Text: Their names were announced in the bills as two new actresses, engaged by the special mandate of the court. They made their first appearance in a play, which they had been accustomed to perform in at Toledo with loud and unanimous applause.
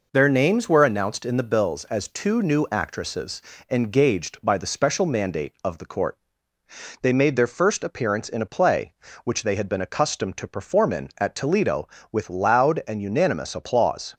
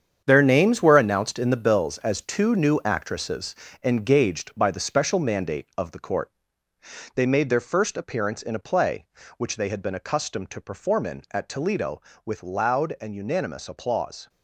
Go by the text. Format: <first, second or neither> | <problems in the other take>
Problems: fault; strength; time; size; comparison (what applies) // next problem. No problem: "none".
first | gets quieter; strong; throughout; 10 dB